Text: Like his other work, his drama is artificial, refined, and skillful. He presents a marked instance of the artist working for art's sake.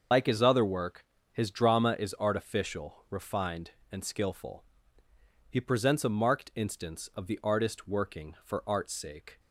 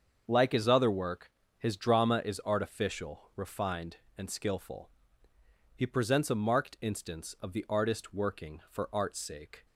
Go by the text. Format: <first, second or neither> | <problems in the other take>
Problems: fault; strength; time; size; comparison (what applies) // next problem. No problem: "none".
second | loses the start of "Like"; at 0.1 s; 95 ms // starts louder than the rest; until 1.4 s; 6.5 dB; also in the second